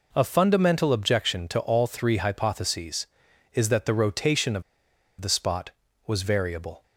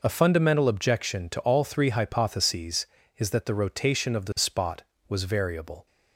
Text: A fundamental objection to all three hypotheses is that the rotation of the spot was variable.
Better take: second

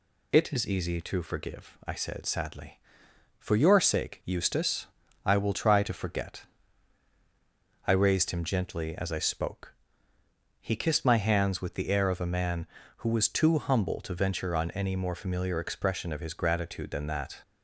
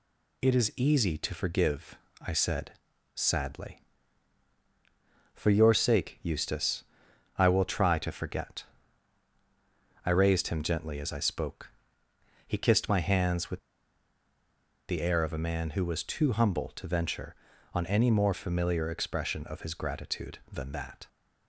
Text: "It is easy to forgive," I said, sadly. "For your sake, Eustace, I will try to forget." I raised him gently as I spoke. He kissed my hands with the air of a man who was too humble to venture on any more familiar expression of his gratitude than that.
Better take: first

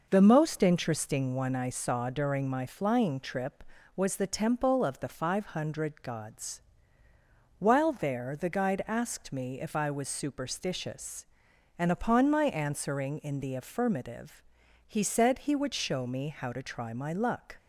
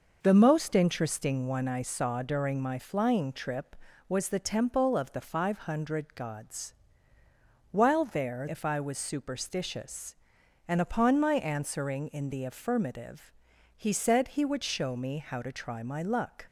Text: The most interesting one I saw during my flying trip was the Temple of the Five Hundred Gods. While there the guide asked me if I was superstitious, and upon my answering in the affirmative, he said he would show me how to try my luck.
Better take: first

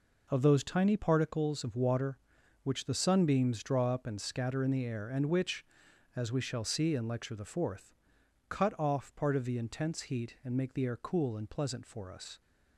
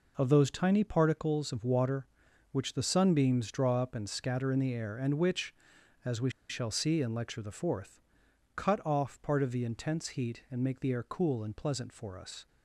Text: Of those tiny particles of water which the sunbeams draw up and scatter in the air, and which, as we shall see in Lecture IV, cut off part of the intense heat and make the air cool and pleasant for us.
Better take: first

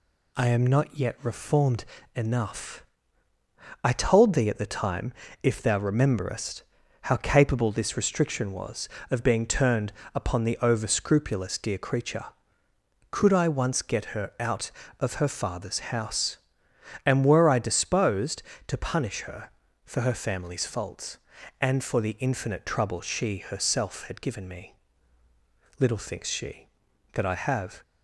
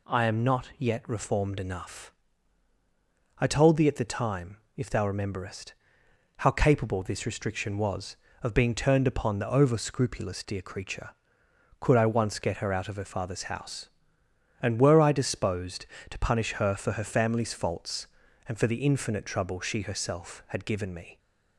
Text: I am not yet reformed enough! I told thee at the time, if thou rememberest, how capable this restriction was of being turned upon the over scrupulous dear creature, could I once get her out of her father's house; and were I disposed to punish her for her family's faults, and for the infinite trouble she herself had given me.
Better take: second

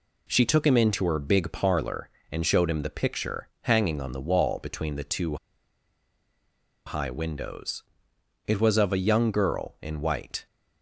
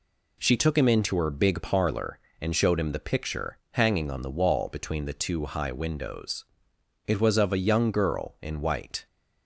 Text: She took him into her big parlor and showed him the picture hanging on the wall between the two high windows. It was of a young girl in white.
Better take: second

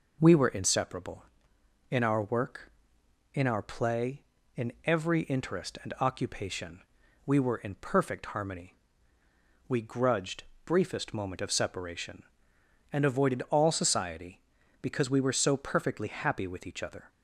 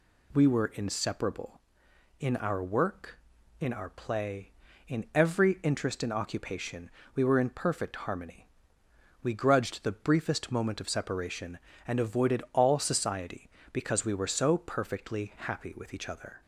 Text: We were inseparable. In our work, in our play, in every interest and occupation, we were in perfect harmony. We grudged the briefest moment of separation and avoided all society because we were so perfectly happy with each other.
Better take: second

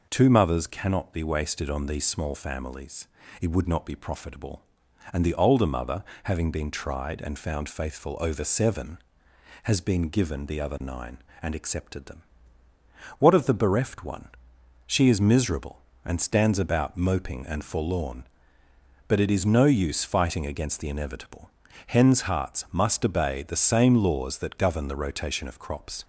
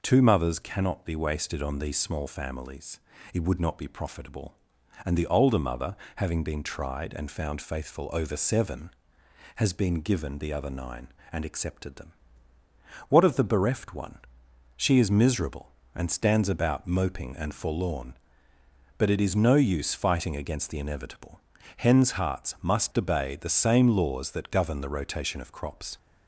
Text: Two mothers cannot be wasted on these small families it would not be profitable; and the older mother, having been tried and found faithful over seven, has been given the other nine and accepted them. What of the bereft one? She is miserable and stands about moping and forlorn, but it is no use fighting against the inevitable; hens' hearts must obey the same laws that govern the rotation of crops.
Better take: neither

